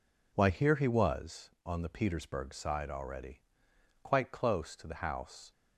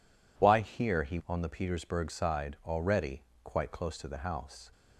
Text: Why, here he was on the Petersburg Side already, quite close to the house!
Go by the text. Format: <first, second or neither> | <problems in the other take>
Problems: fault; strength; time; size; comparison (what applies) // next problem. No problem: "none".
first | skips "was"; at 1.2 s